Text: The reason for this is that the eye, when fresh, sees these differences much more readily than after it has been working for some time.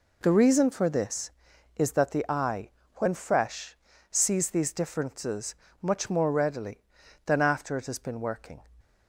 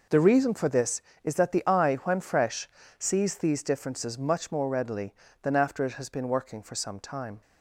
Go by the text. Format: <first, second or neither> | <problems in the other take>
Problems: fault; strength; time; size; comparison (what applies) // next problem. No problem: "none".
second | pauses between "differences" and "much"; slight; at 5.5 s; 0.26 s long // stops before "for some time"; at 8.8 s